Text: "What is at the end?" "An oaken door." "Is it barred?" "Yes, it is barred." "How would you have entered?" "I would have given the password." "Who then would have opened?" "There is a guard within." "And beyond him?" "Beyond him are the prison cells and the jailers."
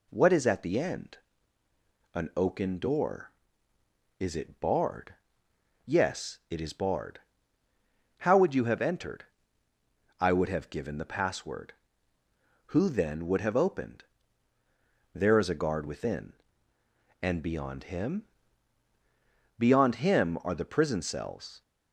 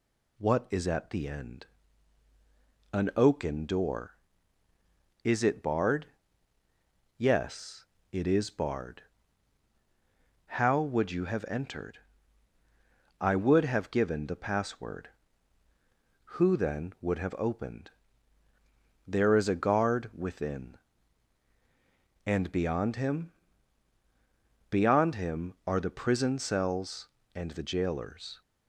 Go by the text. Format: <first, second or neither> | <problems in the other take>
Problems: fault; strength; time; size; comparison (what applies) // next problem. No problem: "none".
second | stops before "and the jailers"; at 21.6 s